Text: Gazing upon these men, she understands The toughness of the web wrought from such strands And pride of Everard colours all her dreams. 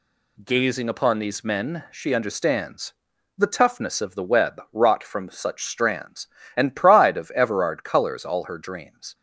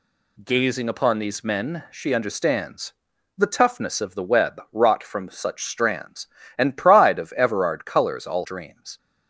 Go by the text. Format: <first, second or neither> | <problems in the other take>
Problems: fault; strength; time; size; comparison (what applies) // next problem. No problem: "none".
first | pauses between "understands" and "The"; noticeable; at 2.9 s; 0.46 s long; noticeable in the first // skips "her"; at 8.4 s